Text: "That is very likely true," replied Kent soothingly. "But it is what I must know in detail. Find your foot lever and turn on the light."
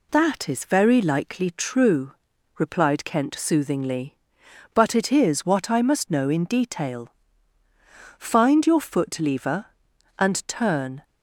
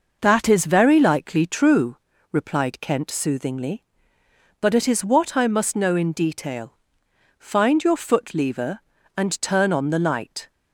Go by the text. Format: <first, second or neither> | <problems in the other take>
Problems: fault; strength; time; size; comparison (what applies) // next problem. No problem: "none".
second | stops before "on the light"; at 11.0 s